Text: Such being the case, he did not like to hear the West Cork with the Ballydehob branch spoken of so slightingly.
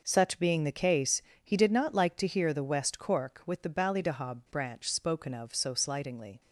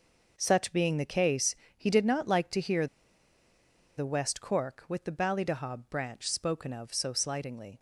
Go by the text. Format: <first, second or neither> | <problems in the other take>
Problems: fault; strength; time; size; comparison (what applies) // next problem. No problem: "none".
first | pauses between "hear" and "the"; at 2.8 s; 1.1 s long